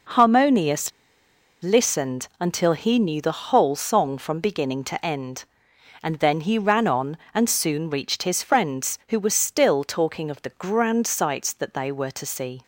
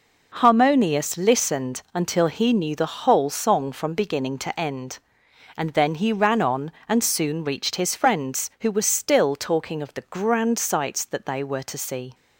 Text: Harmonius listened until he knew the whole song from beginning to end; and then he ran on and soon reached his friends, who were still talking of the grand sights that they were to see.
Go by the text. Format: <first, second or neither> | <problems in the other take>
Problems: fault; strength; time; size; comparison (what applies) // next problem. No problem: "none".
second | pauses between "Harmonius" and "listened"; noticeable; at 0.8 s; 0.72 s long